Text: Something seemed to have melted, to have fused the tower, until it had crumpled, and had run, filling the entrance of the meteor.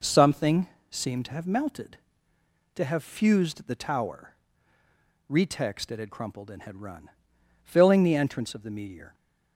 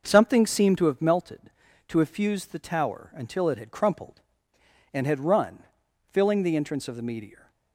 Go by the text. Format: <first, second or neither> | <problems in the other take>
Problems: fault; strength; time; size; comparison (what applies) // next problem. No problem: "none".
second | pauses between "Something" and "seemed"; slight; at 0.6 s; 0.24 s long // says "retext" for "until"; at 5.3 s